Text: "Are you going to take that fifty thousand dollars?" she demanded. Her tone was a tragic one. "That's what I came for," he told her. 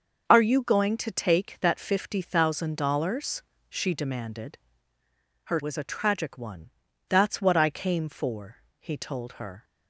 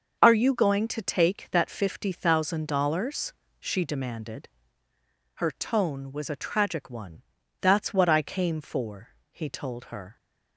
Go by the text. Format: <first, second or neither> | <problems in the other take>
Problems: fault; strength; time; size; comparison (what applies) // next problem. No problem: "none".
second | starts louder than the rest; until 1.2 s; 6.5 dB; also in the second // skips "tone"; at 5.6 s